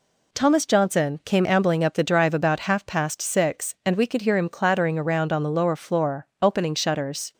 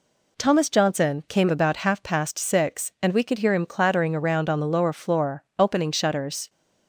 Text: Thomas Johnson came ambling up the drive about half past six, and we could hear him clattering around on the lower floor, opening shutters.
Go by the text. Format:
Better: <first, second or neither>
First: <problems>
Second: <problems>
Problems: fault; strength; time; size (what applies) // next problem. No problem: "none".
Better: first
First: none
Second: skips "ambling up the drive"; at 1.4 s